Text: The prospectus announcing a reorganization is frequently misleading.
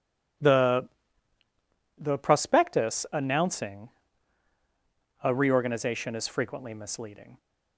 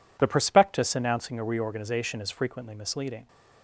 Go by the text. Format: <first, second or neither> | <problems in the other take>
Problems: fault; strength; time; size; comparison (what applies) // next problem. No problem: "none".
second | says "The" twice; at 1.9 s // pauses between "announcing" and "a"; strong; at 3.8 s; 1.3 s long